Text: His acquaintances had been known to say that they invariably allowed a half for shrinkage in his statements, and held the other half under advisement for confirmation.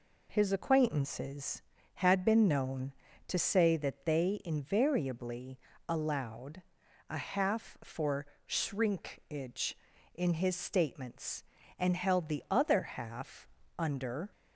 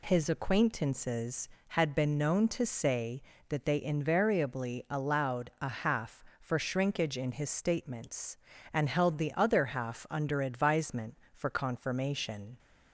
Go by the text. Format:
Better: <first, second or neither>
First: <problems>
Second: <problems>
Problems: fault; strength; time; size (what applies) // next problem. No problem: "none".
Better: second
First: pauses between "invariably" and "allowed"; slight; at 5.5 s; 0.30 s long // pauses between "allowed" and "a"; noticeable; at 6.6 s; 0.46 s long // pauses between "for" and "shrinkage"; slight; at 8.2 s; 0.20 s long // pauses between "half" and "under"; slight; at 13.4 s; 0.28 s long // stops before "advisement for confirmation"; at 14.3 s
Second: none